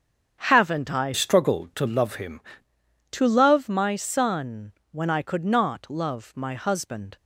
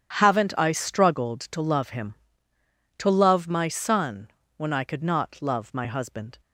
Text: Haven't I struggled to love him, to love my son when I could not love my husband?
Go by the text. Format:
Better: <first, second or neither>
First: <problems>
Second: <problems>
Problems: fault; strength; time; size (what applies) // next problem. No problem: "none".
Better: second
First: starts louder than the rest; strong; until 1.4 s; 7.5 dB // changes voice from "struggled" to "him"; from 1.1 to 2.3 s; 1.2 s long // pauses between "son" and "when"; slight; at 4.7 s; 0.20 s long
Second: pauses between "son" and "when"; slight; at 4.2 s; 0.30 s long